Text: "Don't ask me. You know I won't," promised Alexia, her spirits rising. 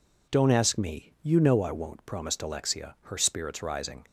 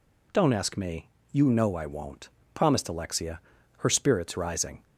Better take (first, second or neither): neither